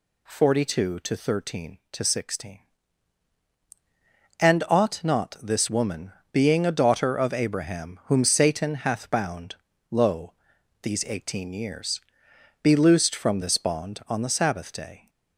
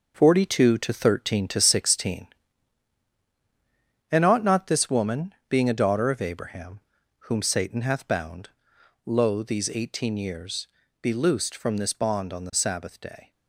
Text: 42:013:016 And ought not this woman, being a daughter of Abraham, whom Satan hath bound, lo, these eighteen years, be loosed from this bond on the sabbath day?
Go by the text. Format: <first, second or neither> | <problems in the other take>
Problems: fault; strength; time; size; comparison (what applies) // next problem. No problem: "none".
first | gets quieter; strong; throughout; 8 dB